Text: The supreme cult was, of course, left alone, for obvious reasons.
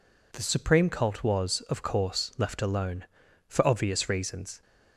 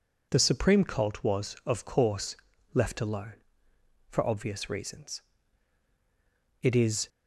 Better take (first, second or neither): first